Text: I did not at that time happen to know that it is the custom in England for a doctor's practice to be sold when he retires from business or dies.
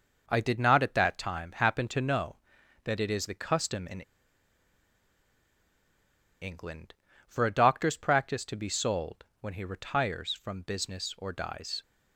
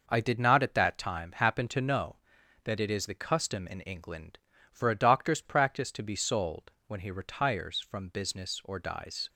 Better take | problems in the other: second | pauses between "in" and "England"; strong; at 3.9 s; 2.4 s long // pauses between "sold" and "when"; slight; at 9.2 s; 0.16 s long; slight in the second

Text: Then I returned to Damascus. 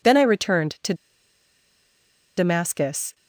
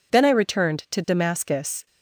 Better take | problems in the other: second | pauses between "to" and "Damascus"; strong; at 0.9 s; 1.4 s long

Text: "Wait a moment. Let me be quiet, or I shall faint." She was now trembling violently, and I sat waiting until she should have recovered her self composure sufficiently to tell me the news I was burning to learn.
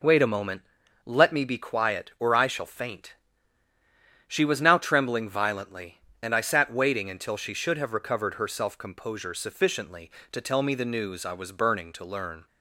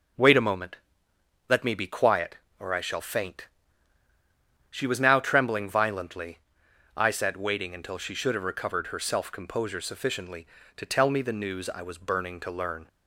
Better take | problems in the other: first | skips "and"; at 6.6 s

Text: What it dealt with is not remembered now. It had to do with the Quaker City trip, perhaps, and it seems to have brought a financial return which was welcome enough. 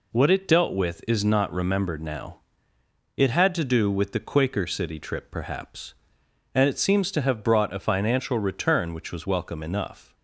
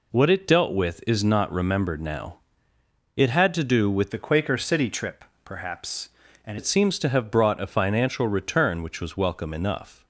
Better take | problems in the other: first | changes voice from "the" to "and"; from 4.1 to 6.5 s; 2.4 s long

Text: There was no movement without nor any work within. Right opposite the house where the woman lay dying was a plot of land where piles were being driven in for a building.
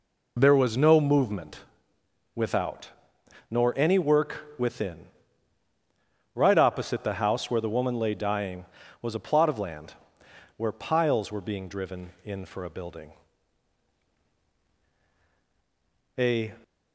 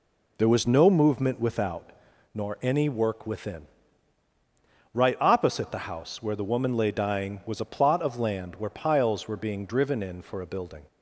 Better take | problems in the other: second | pauses between "movement" and "without"; noticeable; at 1.6 s; 0.74 s long // pauses between "without" and "nor"; noticeable; at 2.8 s; 0.60 s long; also in the second // pauses between "land" and "where"; noticeable; at 9.9 s; 0.62 s long // goes on to say "A"; slight; from 16.1 s on; 0.32 s long

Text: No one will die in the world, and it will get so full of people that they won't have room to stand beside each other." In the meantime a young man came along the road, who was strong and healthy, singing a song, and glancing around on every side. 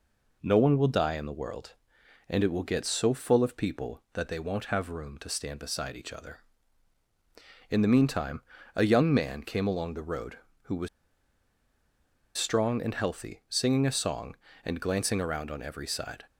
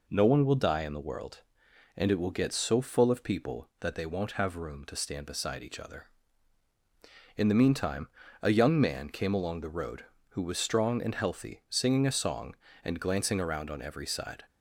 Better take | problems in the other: second | pauses between "meantime" and "a"; slight; at 8.4 s; 0.34 s long; slight in the second // pauses between "was" and "strong"; strong; at 10.8 s; 1.4 s long

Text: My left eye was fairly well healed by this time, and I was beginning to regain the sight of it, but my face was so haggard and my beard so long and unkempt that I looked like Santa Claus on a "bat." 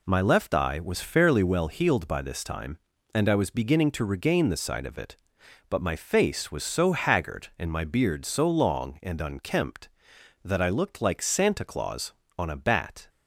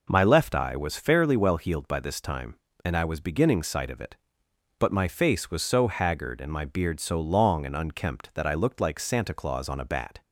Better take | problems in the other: first | skips "to regain the"; at 3.6 s

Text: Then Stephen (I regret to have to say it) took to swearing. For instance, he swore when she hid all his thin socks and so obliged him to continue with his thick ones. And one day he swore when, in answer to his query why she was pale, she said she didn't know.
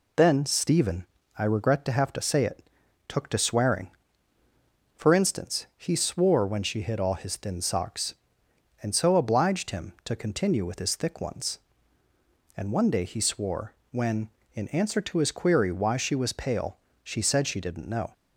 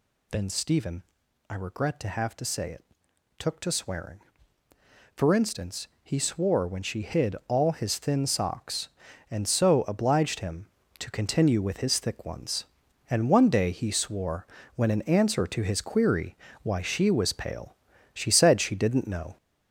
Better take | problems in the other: first | gets louder; noticeable; throughout; 5 dB // pauses between "swore" and "when"; slight; at 14.4 s; 0.30 s long; slight in the first // pauses between "query" and "why"; slight; at 16.3 s; 0.26 s long

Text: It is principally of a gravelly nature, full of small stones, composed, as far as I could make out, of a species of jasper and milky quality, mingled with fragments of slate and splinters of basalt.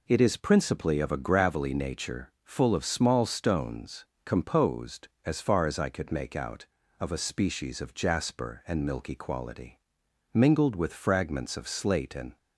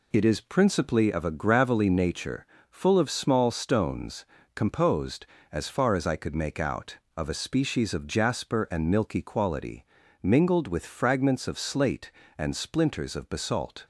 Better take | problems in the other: second | stops before "splinters of basalt"; at 12.3 s

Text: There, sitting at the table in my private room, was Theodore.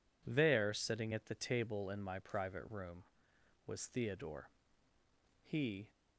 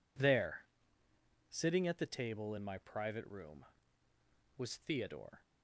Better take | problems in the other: second | goes on to say "He"; slight; from 5.4 s on; 0.48 s long

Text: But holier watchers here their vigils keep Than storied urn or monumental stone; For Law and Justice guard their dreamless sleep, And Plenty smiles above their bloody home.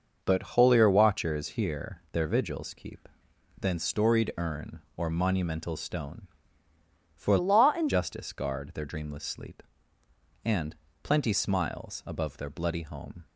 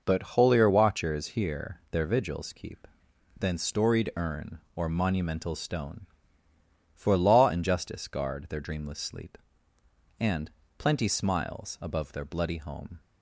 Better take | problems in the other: second | changes voice from "Law" to "and"; from 7.3 to 7.8 s; 0.5 s long // pauses between "And" and "Plenty"; slight; at 10.7 s; 0.28 s long; slight in the second

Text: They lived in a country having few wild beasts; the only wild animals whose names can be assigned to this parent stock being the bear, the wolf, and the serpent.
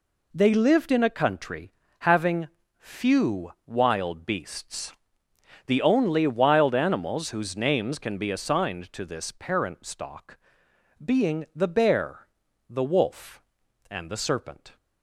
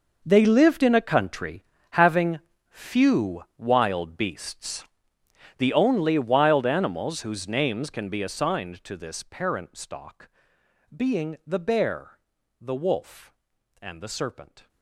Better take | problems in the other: first | gets quieter; strong; throughout; 16.5 dB // pauses between "country" and "having"; slight; at 1.6 s; 0.26 s long; slight in the first // pauses between "having" and "few"; slight; at 2.3 s; 0.32 s long; slight in the first // pauses between "few" and "wild"; slight; at 3.4 s; 0.16 s long; slight in the first // pauses between "stock" and "being"; noticeable; at 10.2 s; 0.68 s long; noticeable in the first

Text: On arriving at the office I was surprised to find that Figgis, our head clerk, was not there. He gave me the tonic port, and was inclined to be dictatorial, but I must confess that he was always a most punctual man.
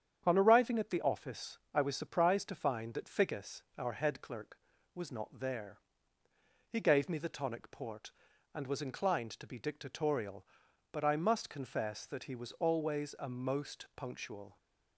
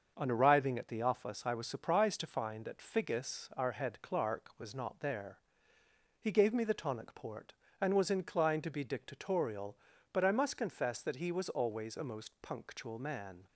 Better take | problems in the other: second | starts louder than the rest; strong; until 1.2 s; 8.5 dB; also in the second // stops before "man"; at 14.5 s

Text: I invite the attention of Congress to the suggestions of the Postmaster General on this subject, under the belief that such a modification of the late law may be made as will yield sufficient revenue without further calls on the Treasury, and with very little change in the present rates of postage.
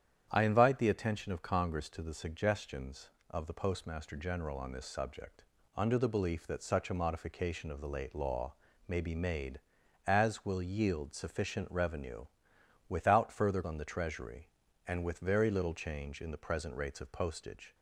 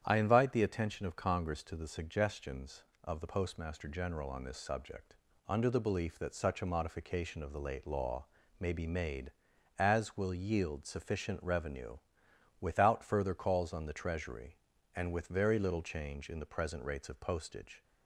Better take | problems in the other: second | starts louder than the rest; strong; until 1.3 s; 9.5 dB; strong in the second // pauses between "law" and "may"; slight; at 8.5 s; 0.34 s long; slight in the second // pauses between "revenue" and "without"; noticeable; at 12.2 s; 0.64 s long; noticeable in the second // skips "calls"; at 13.6 s

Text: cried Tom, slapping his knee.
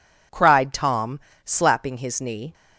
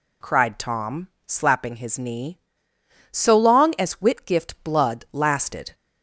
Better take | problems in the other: first | goes on to say "So long as Whitgift blood lasted"; strong; from 3.0 s on; 2.6 s long

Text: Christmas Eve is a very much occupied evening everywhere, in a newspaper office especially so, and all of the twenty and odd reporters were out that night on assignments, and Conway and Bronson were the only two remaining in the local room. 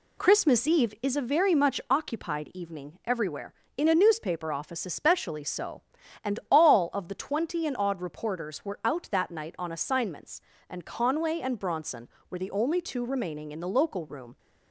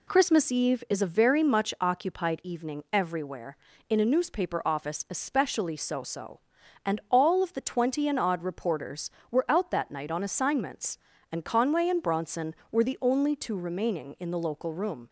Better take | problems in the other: first | says "so" twice; at 6.0 s

